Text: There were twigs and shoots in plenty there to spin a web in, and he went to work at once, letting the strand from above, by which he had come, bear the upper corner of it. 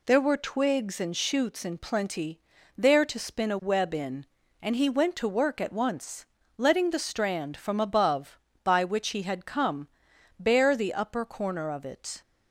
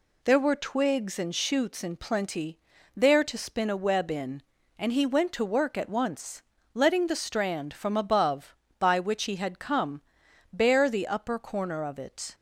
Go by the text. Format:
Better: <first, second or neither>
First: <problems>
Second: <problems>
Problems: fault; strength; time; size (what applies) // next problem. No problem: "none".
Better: neither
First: pauses between "plenty" and "there"; slight; at 2.4 s; 0.36 s long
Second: pauses between "plenty" and "there"; slight; at 2.5 s; 0.36 s long